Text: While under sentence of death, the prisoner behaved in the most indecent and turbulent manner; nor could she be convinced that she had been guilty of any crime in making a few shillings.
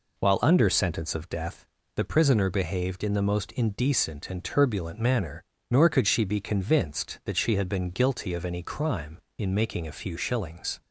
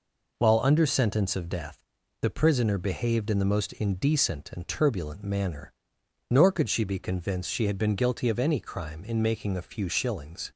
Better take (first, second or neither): first